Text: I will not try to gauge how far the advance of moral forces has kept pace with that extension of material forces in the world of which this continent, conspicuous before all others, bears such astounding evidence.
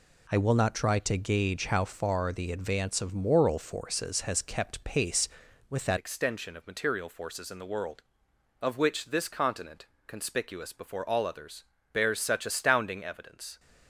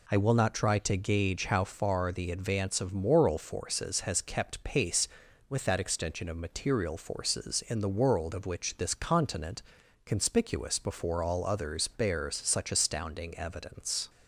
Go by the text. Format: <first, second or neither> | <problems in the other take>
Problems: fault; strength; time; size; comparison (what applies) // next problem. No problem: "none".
second | changes voice at "extension"; from 5.9 s on; 7.6 s long